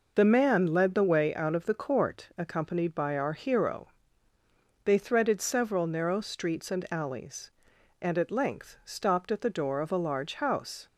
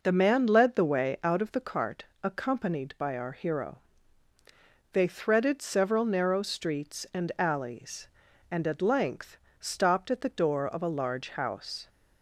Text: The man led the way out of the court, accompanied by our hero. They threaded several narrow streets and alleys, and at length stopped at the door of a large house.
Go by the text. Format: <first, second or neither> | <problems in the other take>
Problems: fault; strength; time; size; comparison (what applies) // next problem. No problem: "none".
first | says "cart" for "court"; at 1.6 s // pauses between "length" and "stopped"; slight; at 9.3 s; 0.22 s long